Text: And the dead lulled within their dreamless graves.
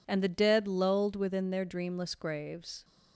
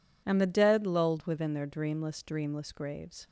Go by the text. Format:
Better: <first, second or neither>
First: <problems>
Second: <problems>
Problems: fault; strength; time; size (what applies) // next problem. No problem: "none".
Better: first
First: none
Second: says "dreamless" twice; at 2.2 s